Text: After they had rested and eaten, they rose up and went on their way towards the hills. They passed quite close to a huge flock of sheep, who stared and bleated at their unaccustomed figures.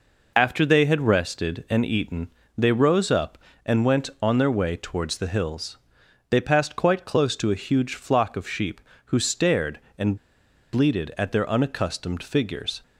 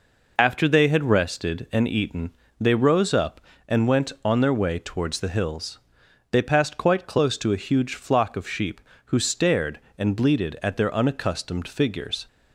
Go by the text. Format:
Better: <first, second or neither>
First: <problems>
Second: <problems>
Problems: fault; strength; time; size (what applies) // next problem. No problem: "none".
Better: second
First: pauses between "and" and "bleated"; noticeable; at 10.1 s; 0.58 s long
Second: none